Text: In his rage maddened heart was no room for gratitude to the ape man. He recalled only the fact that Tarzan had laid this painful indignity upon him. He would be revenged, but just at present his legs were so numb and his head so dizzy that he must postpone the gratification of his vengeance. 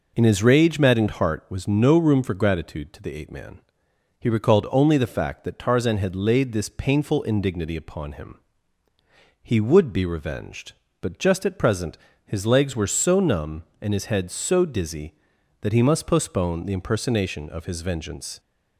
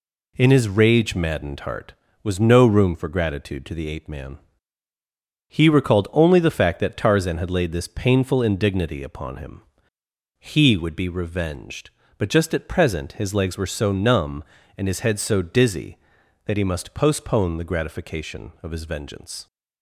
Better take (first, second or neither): second